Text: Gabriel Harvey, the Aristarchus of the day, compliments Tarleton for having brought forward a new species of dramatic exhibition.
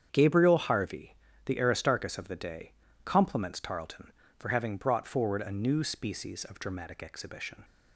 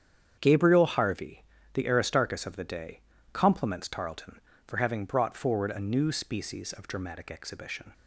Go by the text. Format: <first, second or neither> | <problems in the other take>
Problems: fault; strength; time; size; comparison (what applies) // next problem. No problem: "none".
neither | starts louder than the rest; strong; the same in both